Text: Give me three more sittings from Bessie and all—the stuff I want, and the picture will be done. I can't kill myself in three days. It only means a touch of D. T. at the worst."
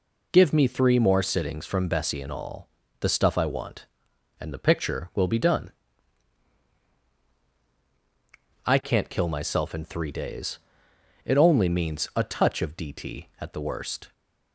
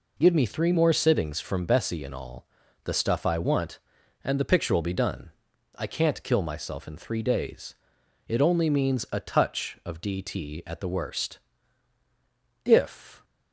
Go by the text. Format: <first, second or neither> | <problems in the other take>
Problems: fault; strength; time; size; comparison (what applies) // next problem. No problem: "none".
first | goes on to say "If"; from 12.6 s on; 0.60 s long